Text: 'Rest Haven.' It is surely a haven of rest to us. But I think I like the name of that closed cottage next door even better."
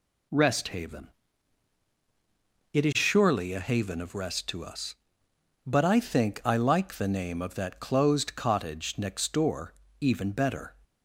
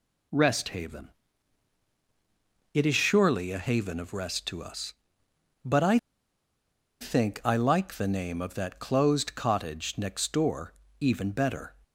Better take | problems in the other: first | pauses between "I" and "think"; at 5.9 s; 1.0 s long // pauses between "door" and "even"; slight; at 10.7 s; 0.26 s long; slight in the first

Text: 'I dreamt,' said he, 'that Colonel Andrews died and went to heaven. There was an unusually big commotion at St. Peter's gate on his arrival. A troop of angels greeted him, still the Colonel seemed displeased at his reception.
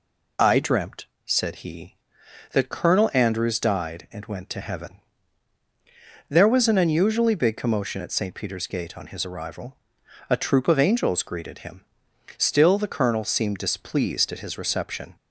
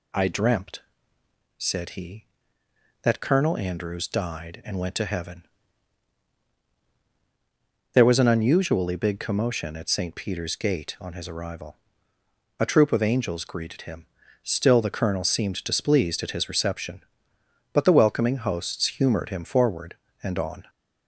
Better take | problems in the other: first | goes on to say "But the welcoming hosts humored him forward and on"; strong; from 17.7 s on; 2.9 s long

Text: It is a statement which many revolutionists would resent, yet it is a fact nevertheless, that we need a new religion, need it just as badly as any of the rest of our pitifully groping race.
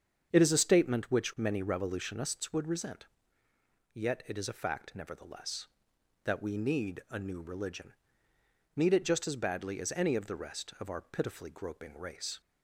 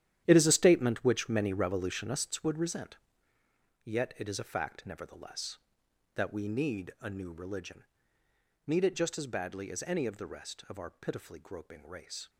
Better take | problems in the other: first | gets quieter; strong; throughout; 12.5 dB // starts louder than the rest; strong; until 1.2 s; 11 dB; strong in the first

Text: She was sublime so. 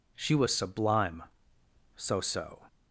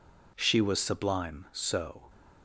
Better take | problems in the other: second | says "so" twice; at 2.1 s

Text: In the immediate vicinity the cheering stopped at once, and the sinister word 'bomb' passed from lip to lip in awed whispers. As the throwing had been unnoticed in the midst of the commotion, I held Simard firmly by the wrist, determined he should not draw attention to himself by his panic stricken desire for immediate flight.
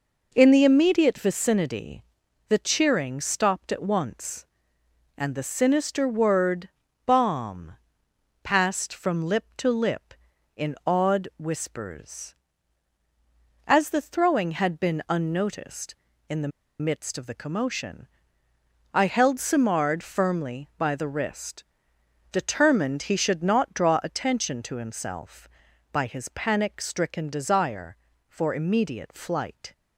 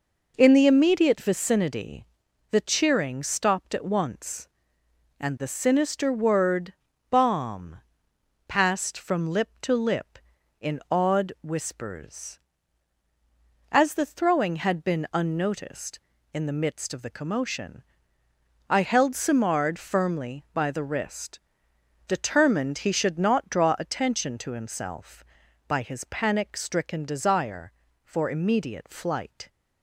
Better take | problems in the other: second | pauses between "vicinity" and "the"; at 2.0 s; 0.44 s long; also in the second // pauses between "word" and "bomb"; slight; at 6.6 s; 0.34 s long; slight in the second // pauses between "bomb" and "passed"; noticeable; at 7.7 s; 0.68 s long; noticeable in the second // pauses between "the" and "midst"; slight; at 16.5 s; 0.31 s long

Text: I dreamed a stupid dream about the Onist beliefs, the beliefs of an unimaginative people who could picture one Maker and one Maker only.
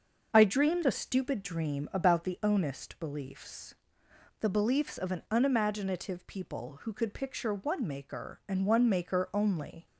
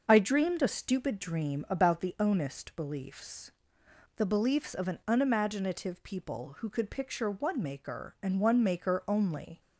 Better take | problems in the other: neither | starts louder than the rest; the same in both

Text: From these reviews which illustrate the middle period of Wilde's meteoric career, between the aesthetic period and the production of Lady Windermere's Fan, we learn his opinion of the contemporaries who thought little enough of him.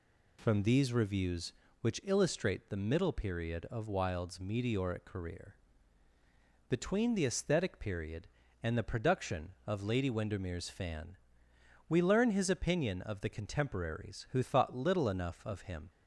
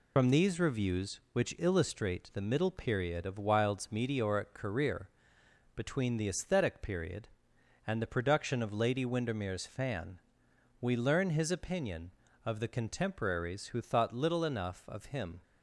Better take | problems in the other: first | loses the start of "From"; at 0.1 s; 70 ms

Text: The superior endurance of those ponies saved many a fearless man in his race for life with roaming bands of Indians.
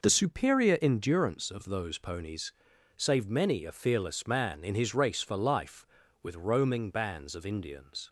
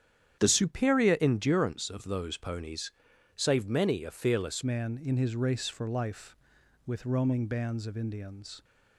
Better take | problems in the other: first | starts louder than the rest; strong; until 1.4 s; 9.5 dB // pauses between "ponies" and "saved"; at 2.9 s; 0.42 s long; also in the first // changes voice at "man"; from 4.6 s on; 4.0 s long

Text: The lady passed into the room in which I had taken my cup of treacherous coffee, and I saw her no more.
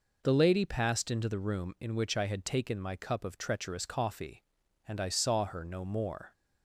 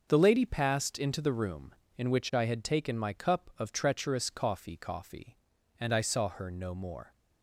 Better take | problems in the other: first | starts louder than the rest; until 1.1 s; 6.5 dB // says "coffee" twice; at 4.7 s

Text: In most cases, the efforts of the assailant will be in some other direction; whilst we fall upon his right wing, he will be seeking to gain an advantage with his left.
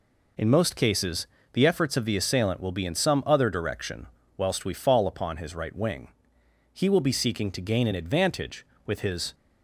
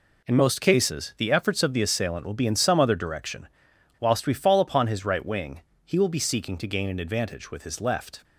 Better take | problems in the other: second | stops before "left"; at 9.3 s

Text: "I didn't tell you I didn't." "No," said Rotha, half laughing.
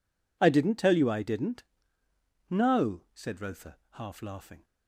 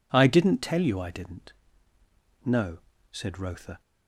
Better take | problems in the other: first | stops before "half laughing"; at 3.8 s

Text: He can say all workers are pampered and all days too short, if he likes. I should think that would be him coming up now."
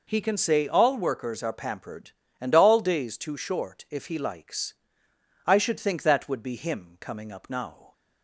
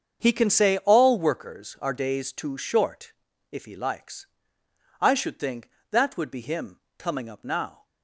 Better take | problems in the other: first | starts louder than the rest; strong; until 1.2 s; 7 dB // skips "pampered and all"; at 1.9 s // pauses between "him" and "coming"; slight; at 6.7 s; 0.22 s long

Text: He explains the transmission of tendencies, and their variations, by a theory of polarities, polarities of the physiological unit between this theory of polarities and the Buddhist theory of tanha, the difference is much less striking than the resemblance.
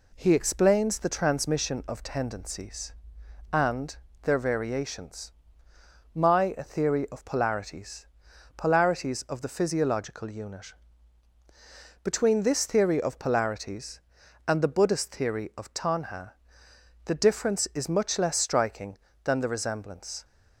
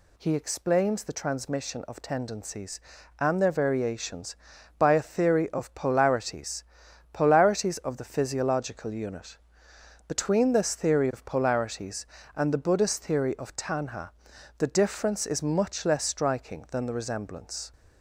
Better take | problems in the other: second | pauses between "and" and "their"; slight; at 3.9 s; 0.26 s long // says "my" for "by"; at 6.1 s // pauses between "unit" and "between"; strong; at 10.7 s; 1.3 s long; noticeable in the second

